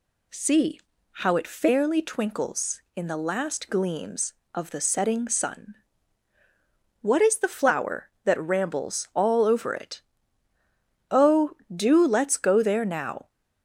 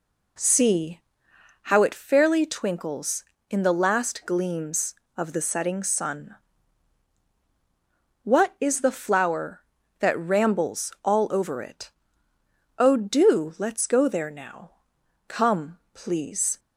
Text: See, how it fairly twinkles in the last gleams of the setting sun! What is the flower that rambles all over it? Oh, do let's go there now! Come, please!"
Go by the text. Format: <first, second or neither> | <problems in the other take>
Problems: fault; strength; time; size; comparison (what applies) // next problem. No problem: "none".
second | stops before "Come please"; at 13.2 s